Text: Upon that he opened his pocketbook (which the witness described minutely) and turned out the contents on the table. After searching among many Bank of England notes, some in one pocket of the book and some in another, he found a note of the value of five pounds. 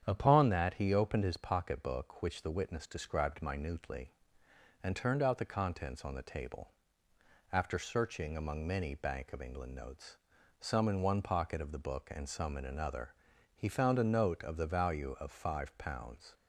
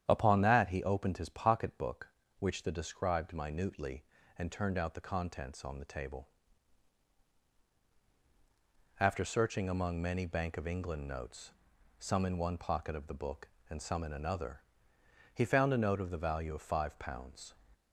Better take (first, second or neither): first